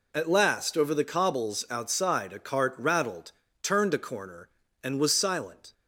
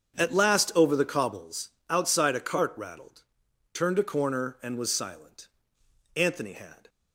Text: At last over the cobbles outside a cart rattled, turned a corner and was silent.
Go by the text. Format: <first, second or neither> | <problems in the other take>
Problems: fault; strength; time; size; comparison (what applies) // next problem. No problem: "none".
first | starts louder than the rest; strong; until 1.2 s; 7.5 dB // pauses between "cobbles" and "outside"; slight; at 1.7 s; 0.18 s long // goes on to say "Anthony had"; noticeable; from 6.1 s on; 0.74 s long